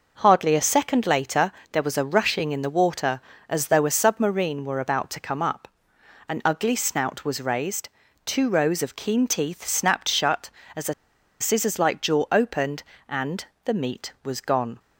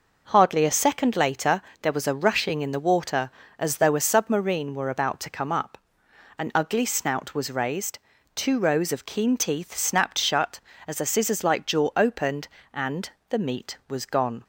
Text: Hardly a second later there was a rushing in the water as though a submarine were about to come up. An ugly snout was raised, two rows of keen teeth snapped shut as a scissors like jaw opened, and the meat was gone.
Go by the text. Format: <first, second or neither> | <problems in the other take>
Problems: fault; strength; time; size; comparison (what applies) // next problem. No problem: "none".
second | pauses between "later" and "there"; slight; at 1.5 s; 0.22 s long; slight in the second // pauses between "a" and "scissors"; noticeable; at 10.9 s; 0.47 s long // pauses between "and" and "the"; slight; at 13.4 s; 0.20 s long; slight in the second